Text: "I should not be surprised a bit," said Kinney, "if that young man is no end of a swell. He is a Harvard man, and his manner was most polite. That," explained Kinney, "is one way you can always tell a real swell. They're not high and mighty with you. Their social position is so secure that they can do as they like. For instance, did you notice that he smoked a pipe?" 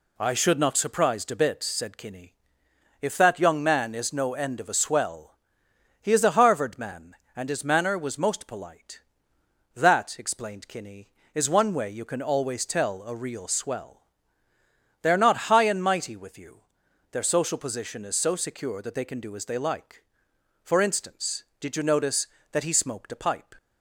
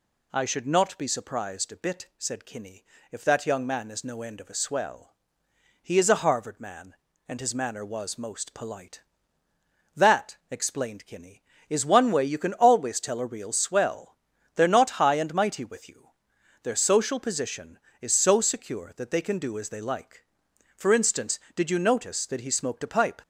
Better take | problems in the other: second | skips "be"; at 0.7 s

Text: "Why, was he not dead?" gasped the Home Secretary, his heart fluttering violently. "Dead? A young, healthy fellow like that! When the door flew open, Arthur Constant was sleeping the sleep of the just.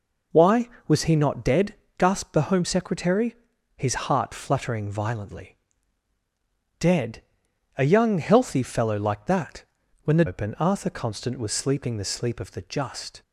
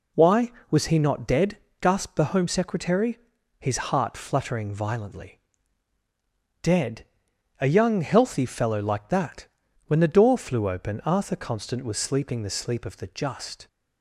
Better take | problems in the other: second | skips "door flew"; at 10.2 s

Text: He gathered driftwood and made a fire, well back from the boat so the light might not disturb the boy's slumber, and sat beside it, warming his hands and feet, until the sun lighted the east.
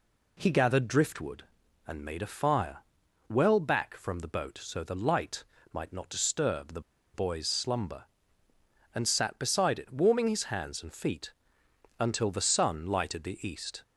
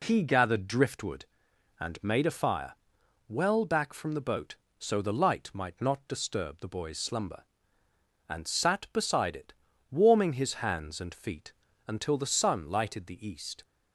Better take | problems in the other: second | pauses between "light" and "might"; slight; at 5.4 s; 0.30 s long // pauses between "the" and "boy's"; slight; at 6.8 s; 0.33 s long

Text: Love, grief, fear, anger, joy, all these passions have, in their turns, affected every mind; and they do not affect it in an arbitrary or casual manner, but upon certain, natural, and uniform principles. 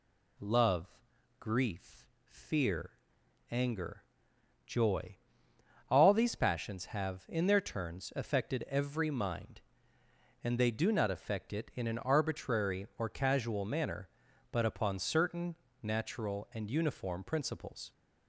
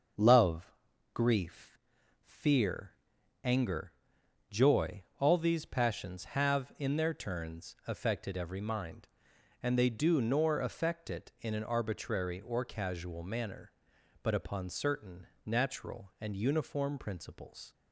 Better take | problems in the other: first | starts louder than the rest; until 1.5 s; 6.5 dB // says "nor" for "not"; at 10.2 s

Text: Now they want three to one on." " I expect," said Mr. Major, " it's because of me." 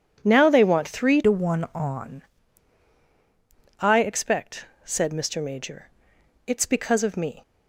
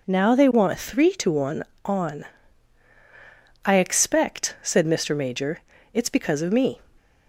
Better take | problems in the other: second | starts louder than the rest; strong; until 1.2 s; 9 dB // changes voice from "to" to "on"; from 1.2 to 2.2 s; 1.0 s long

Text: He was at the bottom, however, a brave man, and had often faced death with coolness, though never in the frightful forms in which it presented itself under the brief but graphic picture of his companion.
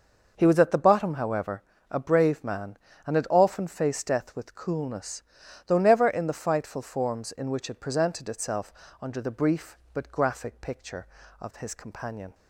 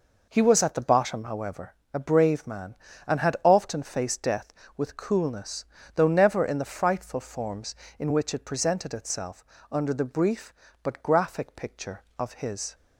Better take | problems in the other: first | pauses between "itself" and "under"; slight; at 9.4 s; 0.26 s long; slight in the first // stops before "companion"; at 12.7 s

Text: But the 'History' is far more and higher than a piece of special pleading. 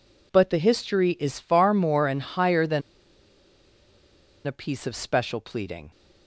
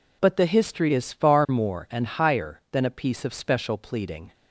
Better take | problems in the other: second | pauses between "than" and "a"; strong; at 2.8 s; 1.6 s long

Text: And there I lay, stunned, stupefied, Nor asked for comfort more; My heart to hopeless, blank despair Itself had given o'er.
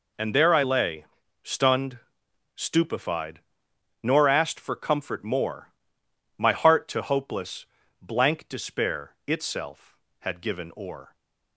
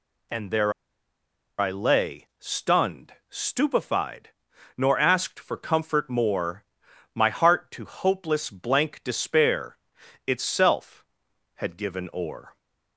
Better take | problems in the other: first | pauses between "there" and "I"; noticeable; at 0.7 s; 0.86 s long // pauses between "despair" and "Itself"; noticeable; at 9.7 s; 0.50 s long

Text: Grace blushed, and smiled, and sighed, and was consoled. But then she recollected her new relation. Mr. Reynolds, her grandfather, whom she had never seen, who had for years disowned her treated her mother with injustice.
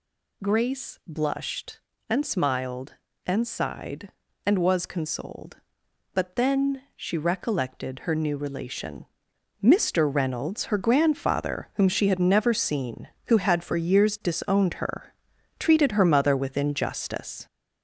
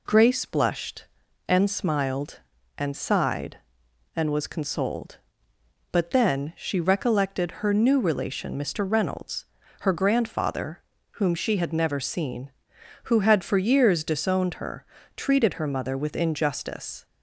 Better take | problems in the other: second | gets louder; noticeable; throughout; 5 dB // pauses between "her" and "treated"; noticeable; at 15.0 s; 0.54 s long; slight in the second

